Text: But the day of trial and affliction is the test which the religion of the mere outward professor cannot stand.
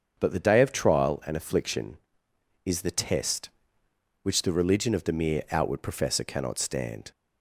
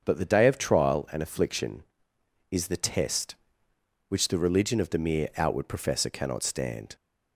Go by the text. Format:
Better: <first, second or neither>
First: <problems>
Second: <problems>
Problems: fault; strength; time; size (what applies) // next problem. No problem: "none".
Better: neither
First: starts louder than the rest; until 1.2 s; 7 dB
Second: starts louder than the rest; until 1.0 s; 7 dB